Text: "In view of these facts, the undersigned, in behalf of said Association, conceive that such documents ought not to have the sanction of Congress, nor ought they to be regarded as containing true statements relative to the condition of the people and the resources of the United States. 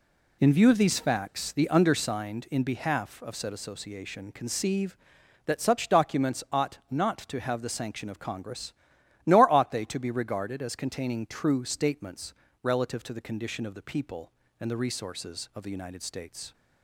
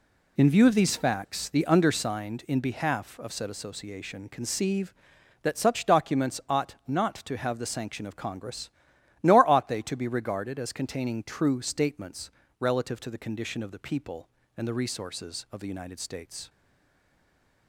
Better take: first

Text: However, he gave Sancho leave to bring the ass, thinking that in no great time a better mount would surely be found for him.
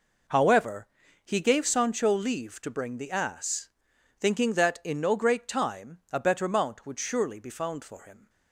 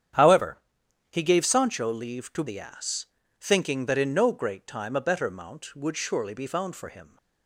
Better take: first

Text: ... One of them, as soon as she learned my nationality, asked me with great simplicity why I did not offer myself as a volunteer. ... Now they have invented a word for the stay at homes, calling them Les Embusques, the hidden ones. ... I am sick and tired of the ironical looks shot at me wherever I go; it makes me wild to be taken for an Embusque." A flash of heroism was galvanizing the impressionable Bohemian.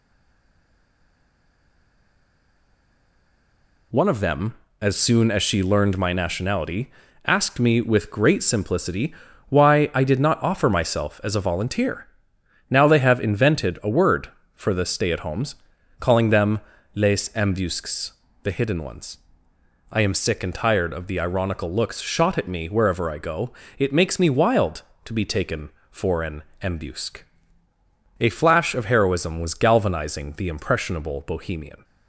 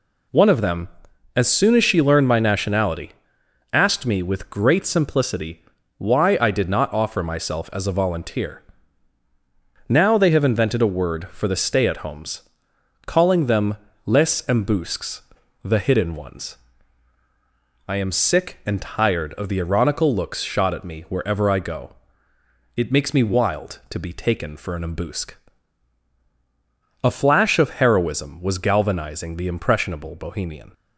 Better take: second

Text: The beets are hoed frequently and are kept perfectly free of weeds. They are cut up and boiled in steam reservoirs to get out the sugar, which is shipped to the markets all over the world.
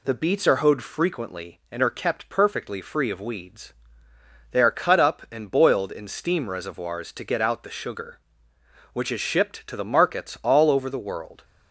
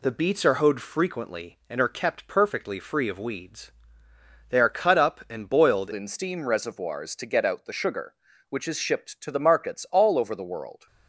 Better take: first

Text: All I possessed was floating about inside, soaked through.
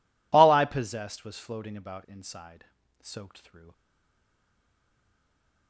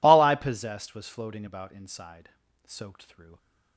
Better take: second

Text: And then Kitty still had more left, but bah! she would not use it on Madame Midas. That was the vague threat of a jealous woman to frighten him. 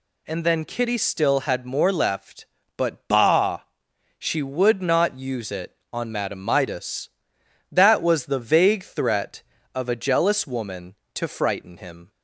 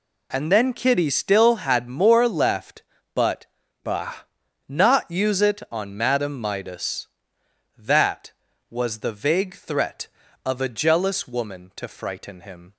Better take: first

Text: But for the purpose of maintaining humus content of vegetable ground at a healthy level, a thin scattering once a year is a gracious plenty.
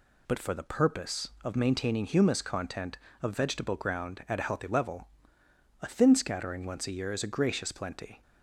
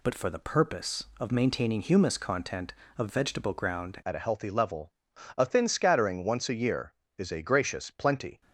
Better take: first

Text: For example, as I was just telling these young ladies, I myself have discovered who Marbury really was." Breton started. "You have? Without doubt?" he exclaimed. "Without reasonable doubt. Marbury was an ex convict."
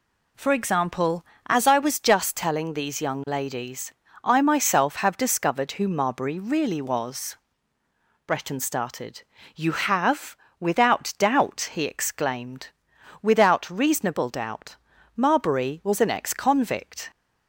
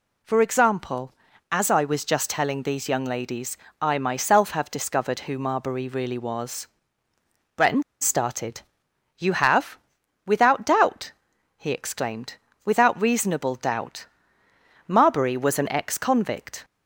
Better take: first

